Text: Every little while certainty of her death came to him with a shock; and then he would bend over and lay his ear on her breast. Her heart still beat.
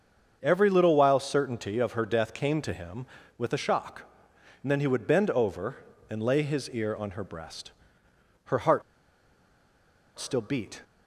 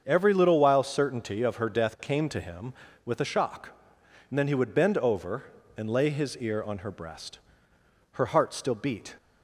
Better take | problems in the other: second | starts louder than the rest; until 1.4 s; 7 dB; also in the second // pauses between "heart" and "still"; strong; at 8.8 s; 1.3 s long

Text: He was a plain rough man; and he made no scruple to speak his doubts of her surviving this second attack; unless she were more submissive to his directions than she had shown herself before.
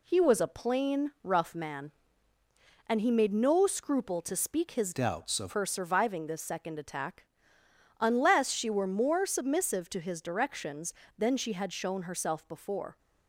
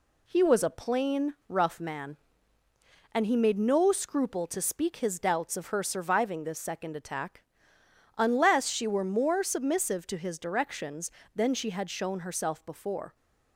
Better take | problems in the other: second | changes voice from "doubts" to "of"; from 4.9 to 5.5 s; 0.6 s long

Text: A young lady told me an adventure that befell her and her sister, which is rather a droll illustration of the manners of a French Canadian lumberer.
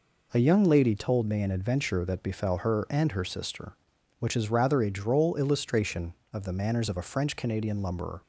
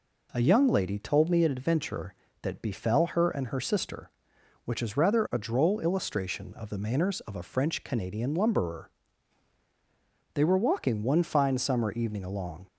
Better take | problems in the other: first | goes on to say "They were walking one fine summer evening along"; strong; from 10.3 s on; 2.3 s long

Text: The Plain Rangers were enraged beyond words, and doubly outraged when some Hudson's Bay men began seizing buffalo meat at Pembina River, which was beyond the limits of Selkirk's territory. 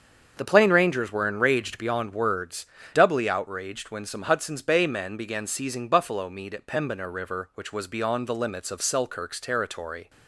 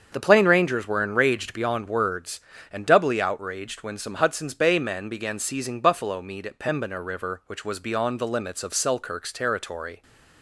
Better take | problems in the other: second | starts louder than the rest; strong; until 1.3 s; 7 dB; also in the second // skips "and"; at 2.8 s

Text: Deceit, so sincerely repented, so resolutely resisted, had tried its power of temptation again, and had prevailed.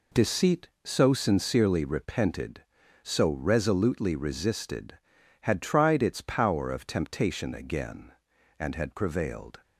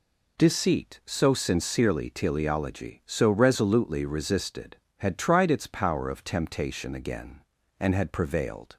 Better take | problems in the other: first | says "teleology" for "repented"; at 2.0 s

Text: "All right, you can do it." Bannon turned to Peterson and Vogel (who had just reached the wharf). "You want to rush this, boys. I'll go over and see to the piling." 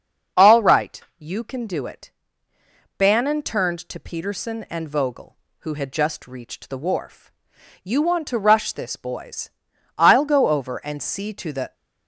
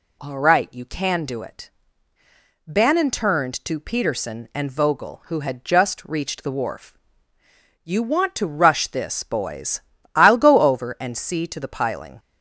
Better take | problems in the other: second | starts louder than the rest; until 1.5 s; 6.5 dB // stops before "piling"; at 11.7 s

